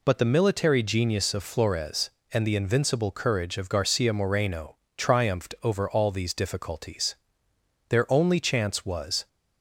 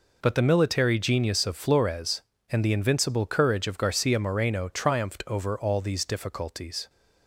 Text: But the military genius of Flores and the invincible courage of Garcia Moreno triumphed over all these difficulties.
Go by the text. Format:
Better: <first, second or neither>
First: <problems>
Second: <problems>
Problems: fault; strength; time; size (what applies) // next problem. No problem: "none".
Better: second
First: pauses between "Moreno" and "triumphed"; slight; at 4.7 s; 0.20 s long // goes on to say "Their only chance was"; from 7.8 s on; 1.3 s long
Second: none